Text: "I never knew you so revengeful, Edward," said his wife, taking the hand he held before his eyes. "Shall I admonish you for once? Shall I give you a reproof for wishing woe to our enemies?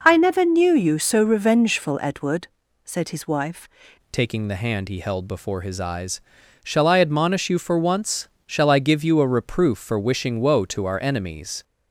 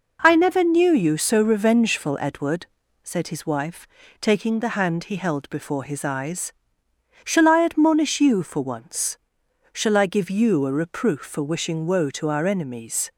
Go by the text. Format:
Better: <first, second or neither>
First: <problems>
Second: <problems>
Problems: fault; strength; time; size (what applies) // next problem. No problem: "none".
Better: second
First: changes voice at "taking"; from 4.1 s on; 7.5 s long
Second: none